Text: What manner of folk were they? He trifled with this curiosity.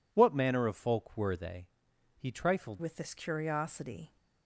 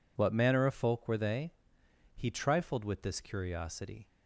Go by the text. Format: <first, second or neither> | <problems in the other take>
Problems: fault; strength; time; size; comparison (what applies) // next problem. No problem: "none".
second | changes voice at "with"; from 2.7 s on; 1.4 s long